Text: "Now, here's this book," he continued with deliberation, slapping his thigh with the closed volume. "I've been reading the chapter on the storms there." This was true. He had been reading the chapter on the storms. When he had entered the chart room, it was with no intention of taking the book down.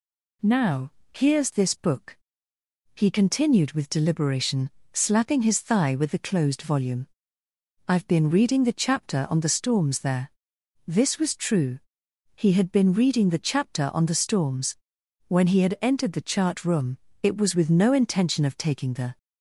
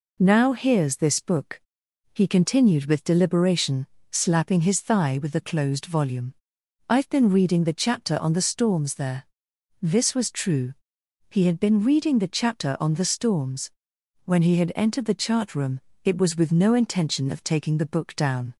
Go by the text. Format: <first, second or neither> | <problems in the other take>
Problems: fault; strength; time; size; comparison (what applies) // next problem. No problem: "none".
second | stops before "book down"; at 19.1 s